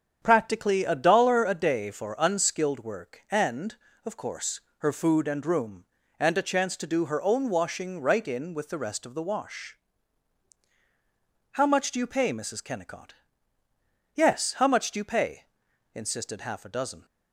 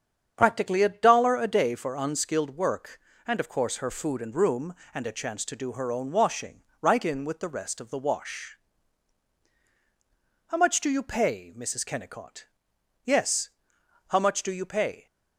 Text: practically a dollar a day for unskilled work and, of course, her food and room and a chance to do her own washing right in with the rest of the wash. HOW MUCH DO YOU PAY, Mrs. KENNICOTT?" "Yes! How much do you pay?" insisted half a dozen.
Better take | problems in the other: first | starts louder than the rest; strong; until 1.3 s; 8 dB; strong in the first // pauses between "washing" and "right"; slight; at 6.6 s; 0.18 s long // stops before "insisted half a dozen"; at 15.0 s

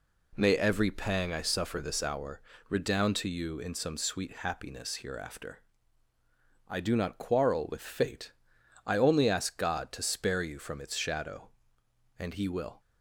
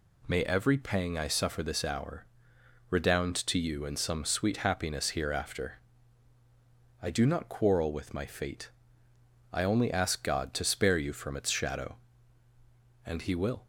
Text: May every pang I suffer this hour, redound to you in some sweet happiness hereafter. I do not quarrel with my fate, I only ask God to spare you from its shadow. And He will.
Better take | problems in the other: second | skips "my"; at 7.8 s

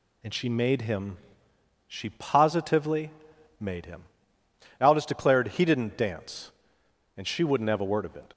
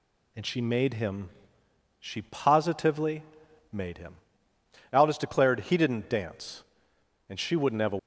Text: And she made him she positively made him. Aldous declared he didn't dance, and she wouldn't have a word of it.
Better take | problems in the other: first | pauses between "him" and "she"; noticeable; at 1.2 s; 0.70 s long; noticeable in the first // pauses between "positively" and "made"; noticeable; at 3.2 s; 0.50 s long; noticeable in the first // stops before "word of it"; at 7.9 s

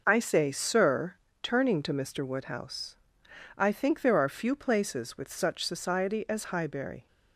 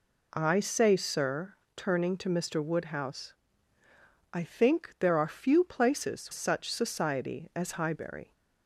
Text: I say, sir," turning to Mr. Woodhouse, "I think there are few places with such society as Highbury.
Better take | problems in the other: first | skips "with"; at 6.3 s

